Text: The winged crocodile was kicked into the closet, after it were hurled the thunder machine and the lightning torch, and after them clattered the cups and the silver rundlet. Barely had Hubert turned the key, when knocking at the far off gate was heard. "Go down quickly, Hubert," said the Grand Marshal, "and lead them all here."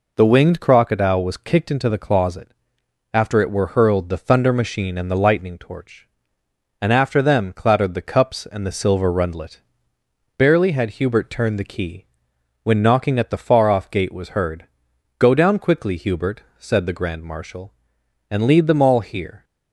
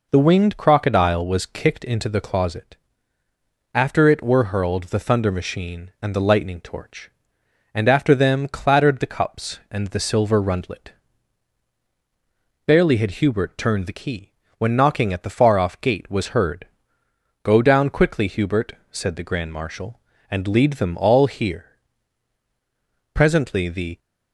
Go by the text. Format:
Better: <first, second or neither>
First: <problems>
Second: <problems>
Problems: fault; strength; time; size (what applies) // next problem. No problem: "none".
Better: first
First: none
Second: goes on to say "Presently the"; noticeable; from 23.1 s on; 0.86 s long